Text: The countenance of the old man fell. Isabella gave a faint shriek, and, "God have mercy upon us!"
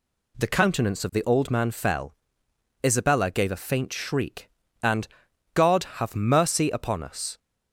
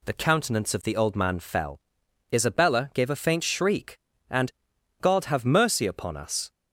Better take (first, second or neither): neither